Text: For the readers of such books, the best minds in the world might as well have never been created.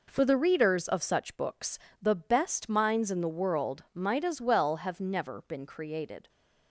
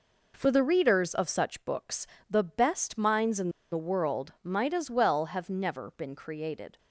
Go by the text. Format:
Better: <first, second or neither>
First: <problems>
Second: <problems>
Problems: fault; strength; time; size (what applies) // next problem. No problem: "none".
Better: first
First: none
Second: pauses between "in" and "the"; slight; at 3.4 s; 0.22 s long